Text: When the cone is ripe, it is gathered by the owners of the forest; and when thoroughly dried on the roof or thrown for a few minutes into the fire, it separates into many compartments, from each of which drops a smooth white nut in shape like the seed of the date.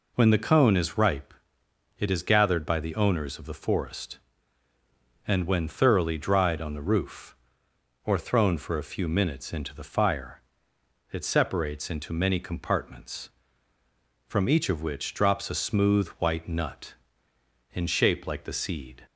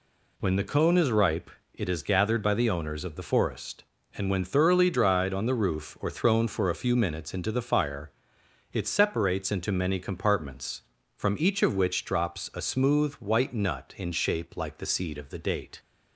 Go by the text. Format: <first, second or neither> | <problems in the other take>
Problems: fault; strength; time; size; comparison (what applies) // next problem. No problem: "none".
second | stops before "of the date"; at 19.0 s